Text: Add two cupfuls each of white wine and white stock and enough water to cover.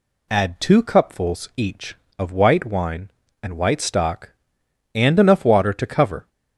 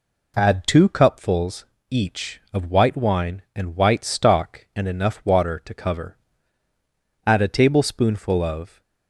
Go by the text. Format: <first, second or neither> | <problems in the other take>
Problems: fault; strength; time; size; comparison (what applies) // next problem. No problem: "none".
first | pauses between "cupfuls" and "each"; slight; at 1.6 s; 0.26 s long // goes on to say "Add a tablespoonful of"; from 7.2 s on; 1.5 s long